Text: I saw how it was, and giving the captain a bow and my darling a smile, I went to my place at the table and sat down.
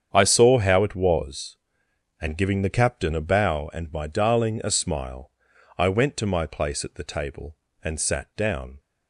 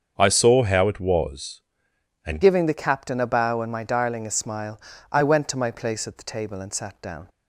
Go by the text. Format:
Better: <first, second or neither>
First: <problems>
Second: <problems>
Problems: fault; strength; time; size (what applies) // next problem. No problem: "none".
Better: first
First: starts louder than the rest; strong; until 1.1 s; 8 dB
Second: starts louder than the rest; until 1.2 s; 7 dB // changes voice at "giving"; from 2.4 s on; 4.8 s long